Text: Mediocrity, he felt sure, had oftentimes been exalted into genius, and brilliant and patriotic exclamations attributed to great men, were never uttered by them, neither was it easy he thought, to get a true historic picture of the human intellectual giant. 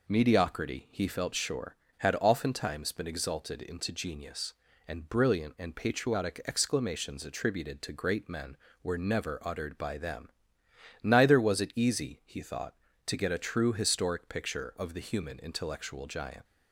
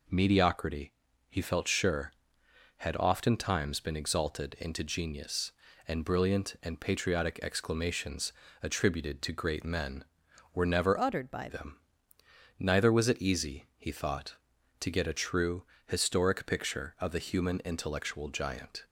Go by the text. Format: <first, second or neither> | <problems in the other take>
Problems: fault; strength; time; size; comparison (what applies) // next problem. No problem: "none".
first | pauses between "exclamations" and "attributed"; slight; at 8.3 s; 0.30 s long // changes voice from "uttered" to "by"; from 10.9 to 11.4 s; 0.5 s long // pauses between "true" and "historic"; slight; at 15.6 s; 0.24 s long